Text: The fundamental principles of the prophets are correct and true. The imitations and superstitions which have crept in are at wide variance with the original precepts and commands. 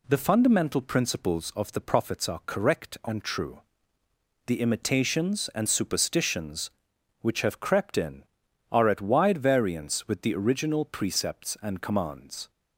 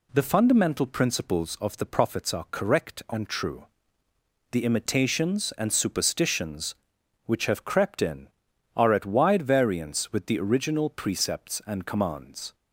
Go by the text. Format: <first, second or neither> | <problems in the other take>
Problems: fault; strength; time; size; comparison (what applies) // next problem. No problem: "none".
neither | none